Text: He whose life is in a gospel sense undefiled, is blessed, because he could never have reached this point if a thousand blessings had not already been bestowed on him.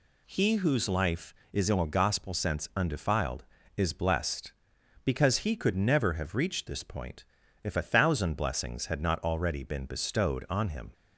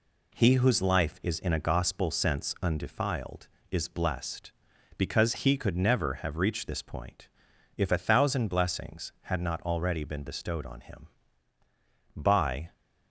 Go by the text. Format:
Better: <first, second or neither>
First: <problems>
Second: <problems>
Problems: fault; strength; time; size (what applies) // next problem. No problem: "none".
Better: first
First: pauses between "point" and "if"; at 7.2 s; 0.40 s long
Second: pauses between "point" and "if"; noticeable; at 7.2 s; 0.48 s long // goes on to say "By"; from 12.1 s on; 0.58 s long